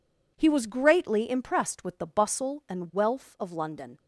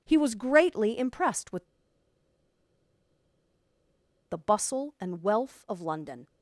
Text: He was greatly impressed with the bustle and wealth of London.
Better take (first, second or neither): first